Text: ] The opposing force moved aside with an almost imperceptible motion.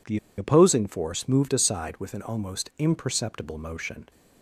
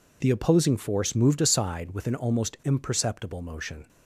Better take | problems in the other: second | pauses between "The" and "opposing"; slight; at 0.1 s; 0.20 s long

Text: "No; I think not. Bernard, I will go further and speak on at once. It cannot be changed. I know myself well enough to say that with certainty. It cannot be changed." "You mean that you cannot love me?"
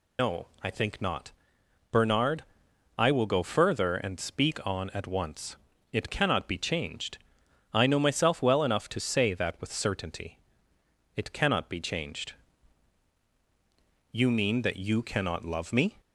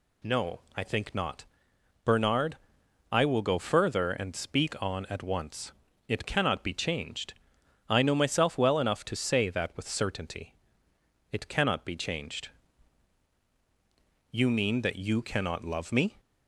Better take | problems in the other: second | loses the start of "No"; at 0.1 s; 85 ms

